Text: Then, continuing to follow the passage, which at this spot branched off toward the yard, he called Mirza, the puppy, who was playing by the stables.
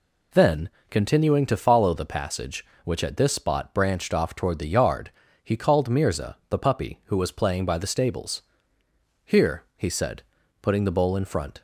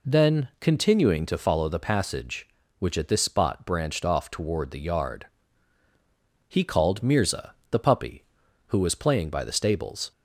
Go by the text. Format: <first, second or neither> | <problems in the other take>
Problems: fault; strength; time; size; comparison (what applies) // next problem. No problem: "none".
second | goes on to say "Here he said putting the bowl in front"; strong; from 9.2 s on; 2.3 s long